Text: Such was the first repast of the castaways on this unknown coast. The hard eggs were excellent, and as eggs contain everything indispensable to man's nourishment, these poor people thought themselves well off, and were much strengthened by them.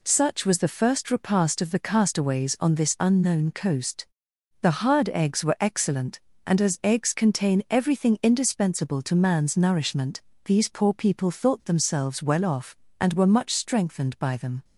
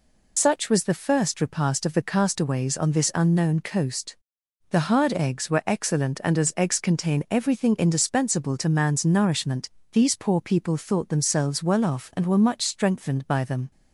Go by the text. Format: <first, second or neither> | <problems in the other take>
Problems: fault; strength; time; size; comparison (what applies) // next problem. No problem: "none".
first | loses the start of "Such"; at 0.3 s; 70 ms